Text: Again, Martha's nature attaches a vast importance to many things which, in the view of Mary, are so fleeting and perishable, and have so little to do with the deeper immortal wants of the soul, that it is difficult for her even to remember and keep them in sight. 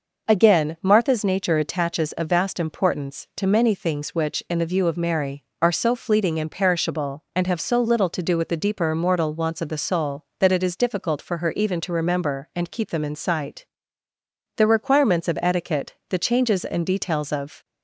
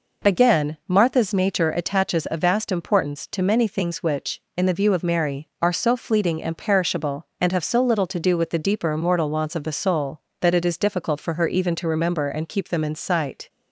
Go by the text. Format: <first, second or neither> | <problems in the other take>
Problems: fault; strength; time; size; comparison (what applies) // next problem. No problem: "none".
second | goes on to say "The requirements of etiquette the changes and details of"; strong; from 14.5 s on; 3.0 s long